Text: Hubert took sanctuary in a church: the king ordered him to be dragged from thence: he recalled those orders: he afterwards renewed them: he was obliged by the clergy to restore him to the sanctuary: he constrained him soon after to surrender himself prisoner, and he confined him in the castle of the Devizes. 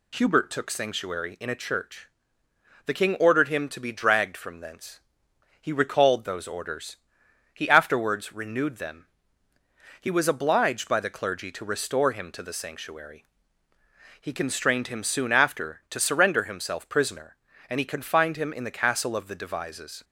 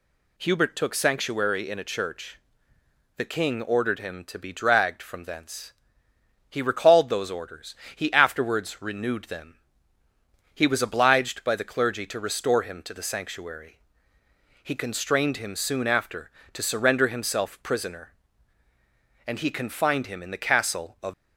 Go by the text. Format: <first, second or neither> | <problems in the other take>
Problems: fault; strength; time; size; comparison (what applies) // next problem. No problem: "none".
first | stops before "the Devizes"; at 21.1 s